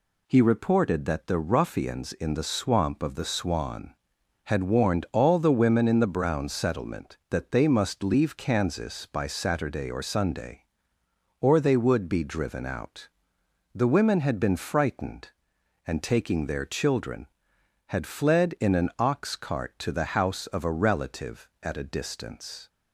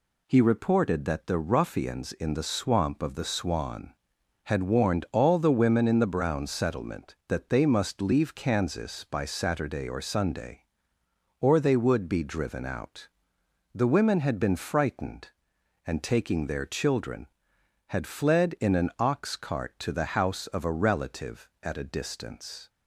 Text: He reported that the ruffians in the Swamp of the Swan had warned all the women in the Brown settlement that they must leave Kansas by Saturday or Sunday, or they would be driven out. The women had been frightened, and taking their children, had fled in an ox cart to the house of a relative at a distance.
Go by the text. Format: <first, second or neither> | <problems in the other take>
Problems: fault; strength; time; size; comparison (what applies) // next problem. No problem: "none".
neither | none